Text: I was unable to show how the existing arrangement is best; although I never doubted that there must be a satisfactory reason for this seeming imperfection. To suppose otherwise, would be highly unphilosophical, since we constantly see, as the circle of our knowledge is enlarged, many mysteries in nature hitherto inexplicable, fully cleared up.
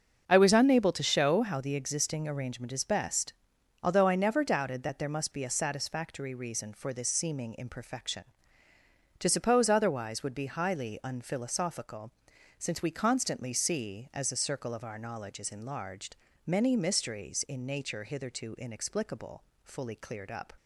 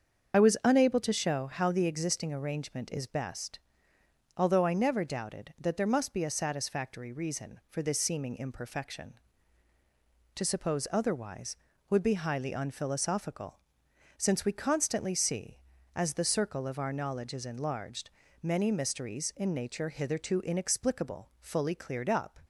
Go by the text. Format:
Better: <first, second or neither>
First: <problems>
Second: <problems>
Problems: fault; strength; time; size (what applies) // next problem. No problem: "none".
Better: first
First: starts louder than the rest; until 1.2 s; 6.5 dB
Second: loses the start of "I"; at 0.3 s; 40 ms // starts louder than the rest; until 1.3 s; 7 dB